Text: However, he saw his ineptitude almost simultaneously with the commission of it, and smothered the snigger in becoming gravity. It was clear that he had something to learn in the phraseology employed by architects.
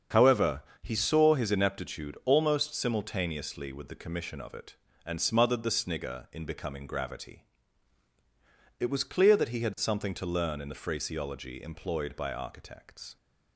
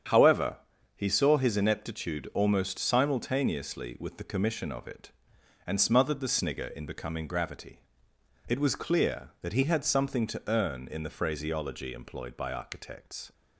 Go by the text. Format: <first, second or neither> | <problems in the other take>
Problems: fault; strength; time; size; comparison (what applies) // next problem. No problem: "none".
first | starts louder than the rest; strong; until 1.4 s; 8 dB; strong in the first // says "earn" for "learn"; at 10.4 s